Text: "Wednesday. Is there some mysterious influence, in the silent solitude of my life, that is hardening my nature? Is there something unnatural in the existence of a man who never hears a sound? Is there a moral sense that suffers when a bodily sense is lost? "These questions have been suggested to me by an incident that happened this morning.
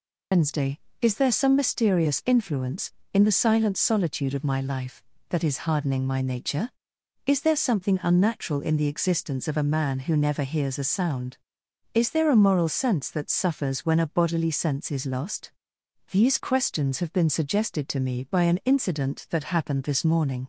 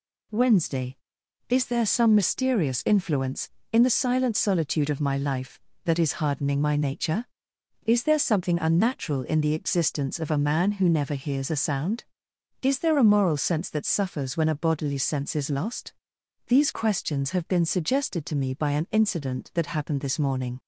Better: second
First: loses the start of "Wednesday"; at 0.3 s; 145 ms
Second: none

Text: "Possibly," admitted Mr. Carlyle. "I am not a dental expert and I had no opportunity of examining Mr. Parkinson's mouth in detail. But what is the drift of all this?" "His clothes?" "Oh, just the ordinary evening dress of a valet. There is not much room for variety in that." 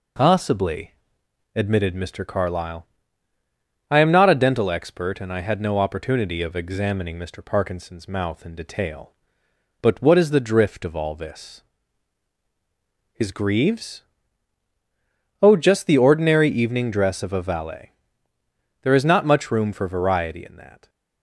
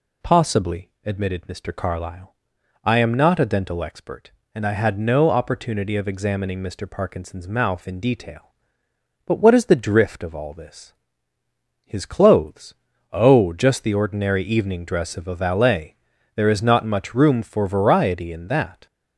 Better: second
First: says "greaves" for "clothes"; at 13.3 s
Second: none

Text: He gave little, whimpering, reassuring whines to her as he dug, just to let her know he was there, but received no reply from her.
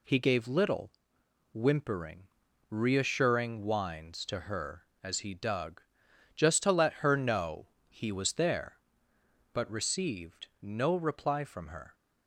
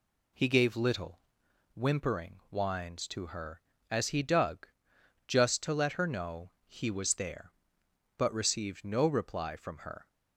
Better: first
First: pauses between "know" and "he"; slight; at 7.6 s; 0.20 s long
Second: skips "reassuring"; at 2.4 s // pauses between "know" and "he"; slight; at 6.4 s; 0.16 s long

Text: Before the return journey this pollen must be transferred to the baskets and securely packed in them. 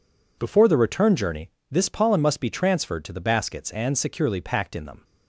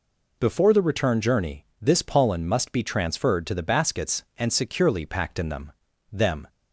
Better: first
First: pauses between "journey" and "this"; slight; at 1.4 s; 0.18 s long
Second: pauses between "journey" and "this"; slight; at 1.6 s; 0.16 s long // says "them" twice; at 6.1 s

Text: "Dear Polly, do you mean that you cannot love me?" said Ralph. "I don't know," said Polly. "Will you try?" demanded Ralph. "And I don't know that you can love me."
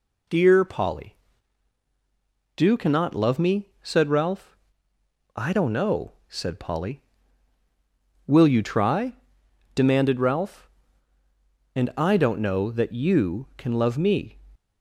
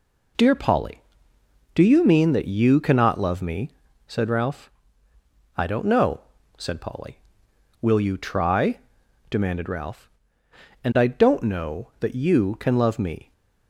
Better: second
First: skips "you mean that you"; at 2.7 s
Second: none

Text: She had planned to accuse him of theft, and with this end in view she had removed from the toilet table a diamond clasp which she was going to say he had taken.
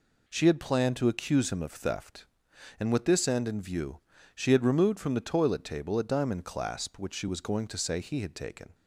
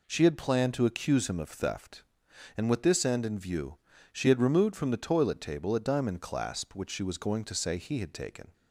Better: neither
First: pauses between "view" and "she"; slight; at 4.0 s; 0.34 s long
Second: pauses between "view" and "she"; slight; at 3.7 s; 0.34 s long

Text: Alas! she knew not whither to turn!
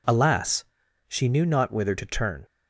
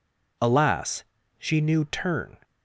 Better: first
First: none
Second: skips "not whither to"; at 1.8 s

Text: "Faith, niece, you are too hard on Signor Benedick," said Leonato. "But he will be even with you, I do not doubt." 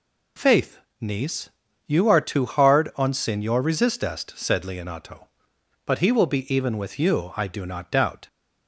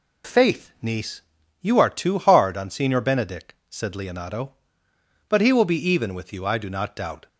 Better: second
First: says "Resistest" for "Benedick"; at 3.6 s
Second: none

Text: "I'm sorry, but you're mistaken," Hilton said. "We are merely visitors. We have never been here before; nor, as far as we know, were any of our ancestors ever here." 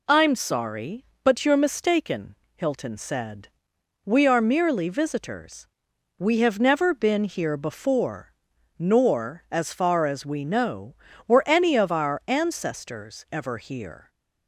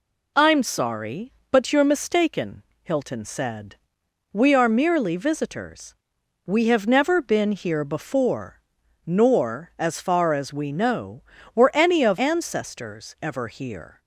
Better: first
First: none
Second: skips "our"; at 12.1 s

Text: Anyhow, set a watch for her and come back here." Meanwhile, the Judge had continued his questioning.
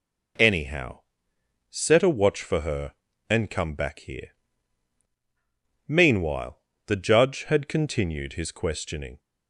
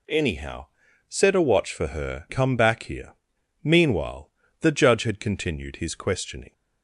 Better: first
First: none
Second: skips "and"; at 2.2 s

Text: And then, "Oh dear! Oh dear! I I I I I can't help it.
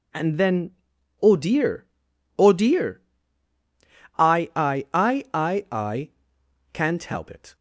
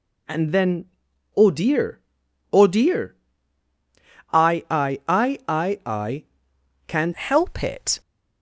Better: first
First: pauses between "I" and "can't"; noticeable; at 6.0 s; 0.64 s long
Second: pauses between "I" and "can't"; noticeable; at 6.2 s; 0.64 s long // changes voice at "help"; from 7.1 s on; 0.9 s long

